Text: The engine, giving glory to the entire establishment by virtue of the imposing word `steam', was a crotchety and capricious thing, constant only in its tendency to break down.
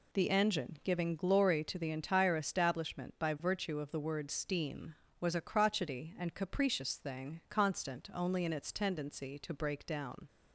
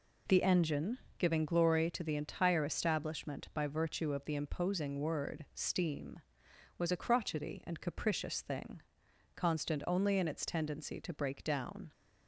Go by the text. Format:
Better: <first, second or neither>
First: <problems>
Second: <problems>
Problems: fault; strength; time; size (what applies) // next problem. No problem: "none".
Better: second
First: skips "imposing"; at 3.9 s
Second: none